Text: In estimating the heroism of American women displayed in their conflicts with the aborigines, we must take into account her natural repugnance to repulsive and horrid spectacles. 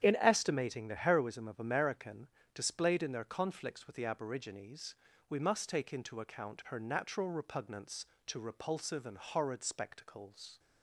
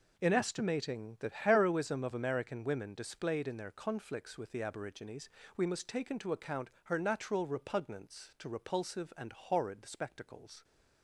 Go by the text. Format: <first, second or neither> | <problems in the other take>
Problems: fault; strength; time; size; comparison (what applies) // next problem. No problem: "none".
second | starts louder than the rest; strong; until 1.0 s; 9 dB // skips "women"; at 2.4 s